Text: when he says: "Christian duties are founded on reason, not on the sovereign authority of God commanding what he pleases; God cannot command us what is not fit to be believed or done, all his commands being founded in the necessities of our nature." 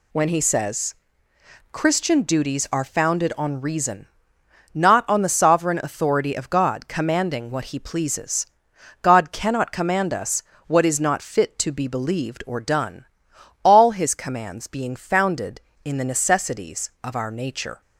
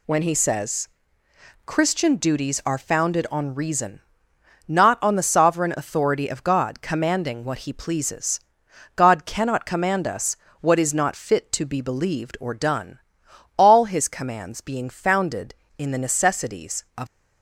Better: first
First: pauses between "us" and "what"; slight; at 10.4 s; 0.24 s long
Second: pauses between "us" and "what"; slight; at 10.3 s; 0.24 s long // stops before "our nature"; at 17.0 s

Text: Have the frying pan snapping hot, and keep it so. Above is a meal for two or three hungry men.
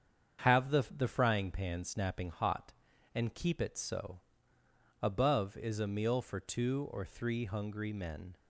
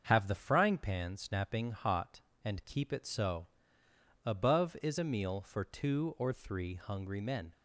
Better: second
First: starts louder than the rest; strong; until 1.4 s; 7.5 dB // says "the" twice; at 0.8 s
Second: starts louder than the rest; until 1.0 s; 7 dB

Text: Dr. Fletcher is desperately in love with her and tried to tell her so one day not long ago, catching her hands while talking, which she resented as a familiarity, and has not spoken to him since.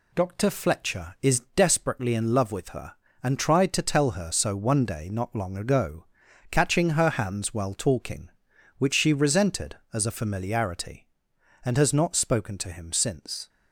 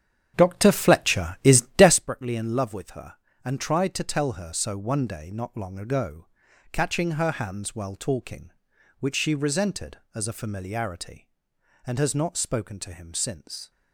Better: first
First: pauses between "is" and "desperately"; slight; at 1.3 s; 0.16 s long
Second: starts louder than the rest; strong; until 2.0 s; 9 dB // pauses between "is" and "desperately"; slight; at 1.5 s; 0.16 s long

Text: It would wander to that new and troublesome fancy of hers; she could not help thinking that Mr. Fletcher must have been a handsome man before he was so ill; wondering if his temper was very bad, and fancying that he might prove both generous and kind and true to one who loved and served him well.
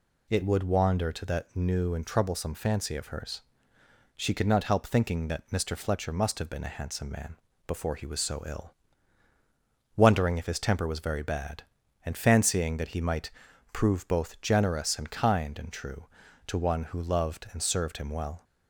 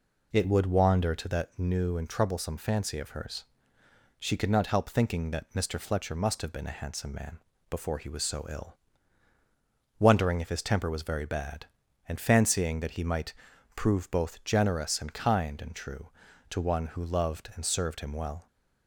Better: first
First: pauses between "man" and "before"; slight; at 7.3 s; 0.28 s long // pauses between "might" and "prove"; at 13.2 s; 0.42 s long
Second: starts louder than the rest; until 1.5 s; 3.5 dB // pauses between "man" and "before"; slight; at 7.4 s; 0.28 s long // pauses between "might" and "prove"; at 13.3 s; 0.42 s long

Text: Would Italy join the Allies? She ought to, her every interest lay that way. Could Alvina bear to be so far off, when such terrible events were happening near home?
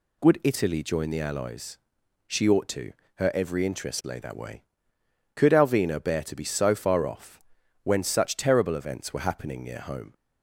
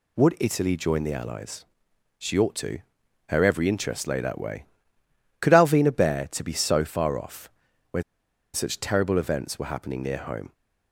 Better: first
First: none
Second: pauses between "when" and "such"; noticeable; at 8.0 s; 0.51 s long

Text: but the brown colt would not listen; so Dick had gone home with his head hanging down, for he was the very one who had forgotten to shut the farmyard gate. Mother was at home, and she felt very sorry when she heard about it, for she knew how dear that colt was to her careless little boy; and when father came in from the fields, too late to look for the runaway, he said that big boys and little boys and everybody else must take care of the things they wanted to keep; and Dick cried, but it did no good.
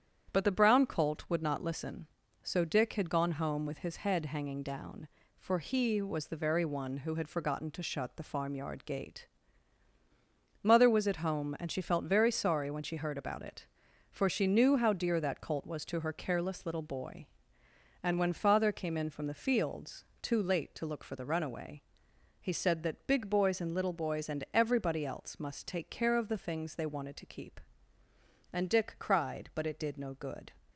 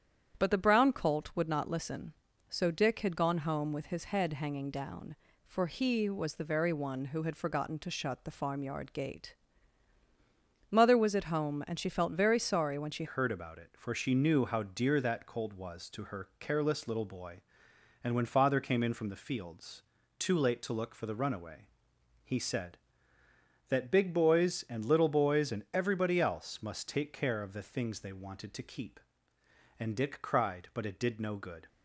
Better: first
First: starts louder than the rest; strong; until 1.3 s; 9 dB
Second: starts louder than the rest; strong; until 1.4 s; 9 dB // changes voice at "heard"; from 13.0 s on; 18.6 s long

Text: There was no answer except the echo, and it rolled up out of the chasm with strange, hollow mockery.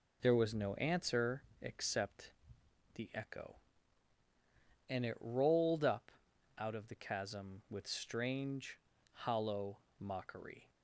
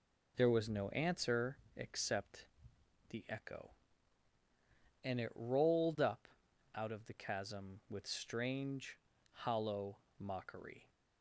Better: neither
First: pauses between "answer" and "except"; slight; at 1.4 s; 0.22 s long // pauses between "except" and "the"; noticeable; at 2.3 s; 0.62 s long // pauses between "up" and "out"; noticeable; at 6.1 s; 0.48 s long // pauses between "hollow" and "mockery"; slight; at 9.7 s; 0.22 s long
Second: pauses between "answer" and "except"; slight; at 1.5 s; 0.22 s long // pauses between "except" and "the"; noticeable; at 2.4 s; 0.62 s long // pauses between "up" and "out"; noticeable; at 6.2 s; 0.48 s long // pauses between "hollow" and "mockery"; slight; at 9.9 s; 0.22 s long

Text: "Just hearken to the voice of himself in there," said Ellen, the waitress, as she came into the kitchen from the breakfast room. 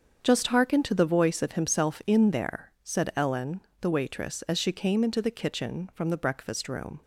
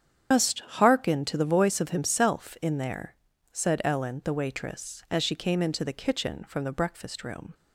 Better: first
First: starts louder than the rest; until 1.2 s; 7 dB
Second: loses the start of "Just"; at 0.3 s; 130 ms // starts louder than the rest; strong; until 1.3 s; 8.5 dB

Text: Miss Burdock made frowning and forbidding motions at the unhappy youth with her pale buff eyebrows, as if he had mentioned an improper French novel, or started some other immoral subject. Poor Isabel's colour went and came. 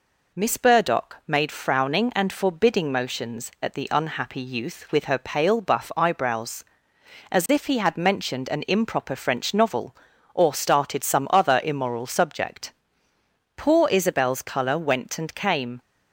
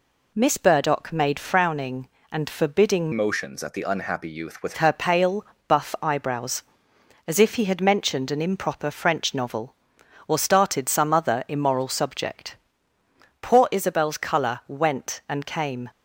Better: first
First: none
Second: changes voice from "motions" to "with"; from 3.1 to 4.7 s; 1.6 s long // pauses between "pale" and "buff"; slight; at 5.4 s; 0.22 s long

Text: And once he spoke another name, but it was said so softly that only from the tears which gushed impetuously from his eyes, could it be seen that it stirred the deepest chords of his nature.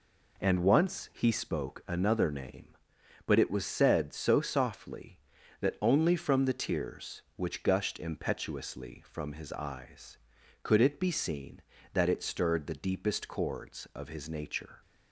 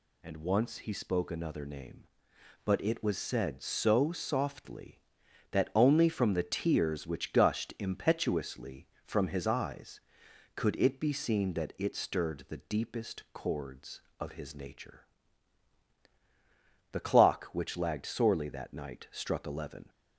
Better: first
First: none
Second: goes on to say "The clock which lagged sorely that night struck eleven"; strong; from 16.9 s on; 2.9 s long

